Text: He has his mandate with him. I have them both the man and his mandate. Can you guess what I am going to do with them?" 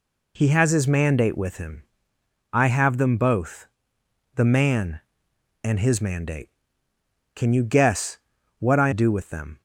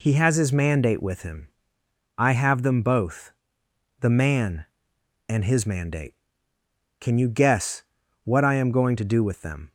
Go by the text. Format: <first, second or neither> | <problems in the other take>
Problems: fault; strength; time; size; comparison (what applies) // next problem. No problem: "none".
second | pauses between "both" and "the"; noticeable; at 3.6 s; 0.68 s long; noticeable in the second // pauses between "guess" and "what"; at 8.1 s; 0.40 s long; also in the second // skips "am going to"; at 8.9 s